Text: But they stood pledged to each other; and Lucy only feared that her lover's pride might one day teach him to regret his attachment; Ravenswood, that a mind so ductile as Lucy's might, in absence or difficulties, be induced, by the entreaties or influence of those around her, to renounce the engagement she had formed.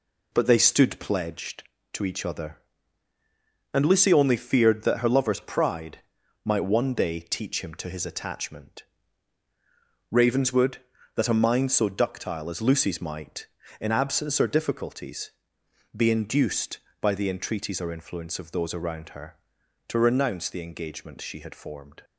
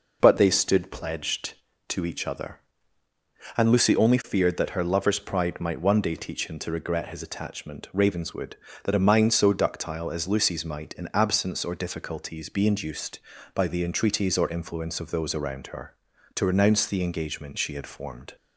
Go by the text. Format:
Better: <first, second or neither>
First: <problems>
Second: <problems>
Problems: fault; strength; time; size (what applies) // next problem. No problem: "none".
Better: second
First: pauses between "pride" and "might"; at 5.9 s; 0.44 s long // skips "regret"; at 7.8 s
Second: none